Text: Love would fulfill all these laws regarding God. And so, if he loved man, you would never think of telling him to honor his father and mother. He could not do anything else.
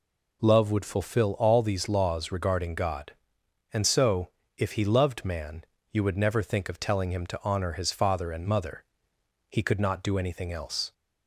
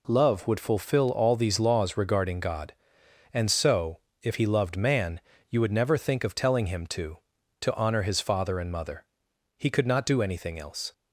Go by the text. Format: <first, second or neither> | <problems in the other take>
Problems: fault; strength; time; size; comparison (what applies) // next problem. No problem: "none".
first | says "to" twice; at 7.6 s